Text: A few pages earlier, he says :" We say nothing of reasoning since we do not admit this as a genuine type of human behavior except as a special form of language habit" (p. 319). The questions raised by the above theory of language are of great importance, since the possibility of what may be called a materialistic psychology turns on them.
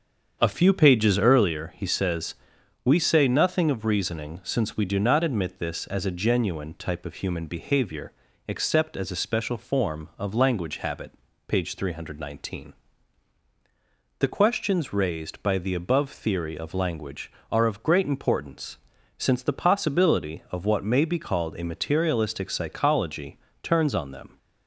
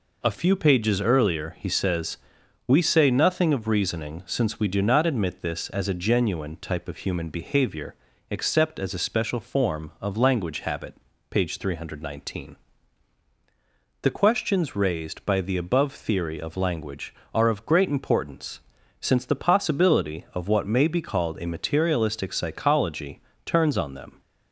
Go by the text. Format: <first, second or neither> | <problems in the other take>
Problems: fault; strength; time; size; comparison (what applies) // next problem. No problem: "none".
second | starts louder than the rest; strong; until 1.5 s; 7.5 dB // pauses between "behavior" and "except"; slight; at 8.1 s; 0.34 s long; slight in the second // pauses between "psychology" and "turns"; slight; at 23.3 s; 0.24 s long; slight in the second